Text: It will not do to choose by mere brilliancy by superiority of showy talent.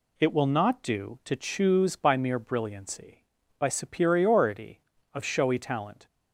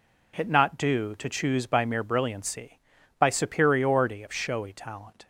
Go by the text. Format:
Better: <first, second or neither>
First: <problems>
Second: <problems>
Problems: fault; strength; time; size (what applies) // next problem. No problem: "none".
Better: first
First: none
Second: skips "will"; at 0.4 s